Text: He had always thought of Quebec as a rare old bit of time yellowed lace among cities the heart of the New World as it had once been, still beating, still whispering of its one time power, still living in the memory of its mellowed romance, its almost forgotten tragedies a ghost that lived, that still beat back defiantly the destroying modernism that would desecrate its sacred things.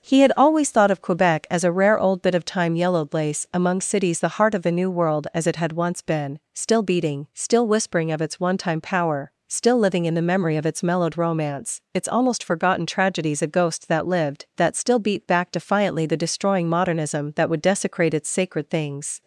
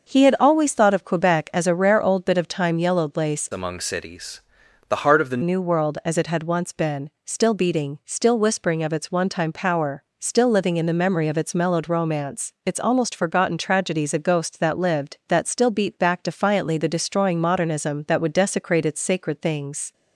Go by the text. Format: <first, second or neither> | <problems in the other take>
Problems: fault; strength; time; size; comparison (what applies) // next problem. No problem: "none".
first | starts louder than the rest; noticeable; until 1.1 s; 6 dB; also in the first // changes voice from "among" to "the"; from 3.5 to 5.4 s; 1.9 s long // pauses between "cities" and "the"; noticeable; at 4.3 s; 0.50 s long